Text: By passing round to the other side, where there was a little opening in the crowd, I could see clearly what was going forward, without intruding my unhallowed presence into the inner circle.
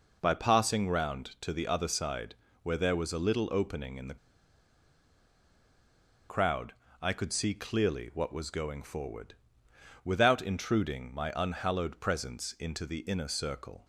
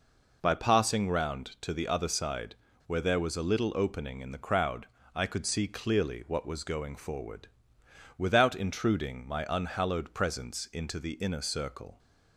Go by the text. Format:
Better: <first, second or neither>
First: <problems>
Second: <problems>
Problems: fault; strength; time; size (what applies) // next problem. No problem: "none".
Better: second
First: pauses between "the" and "crowd"; strong; at 4.1 s; 2.1 s long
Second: none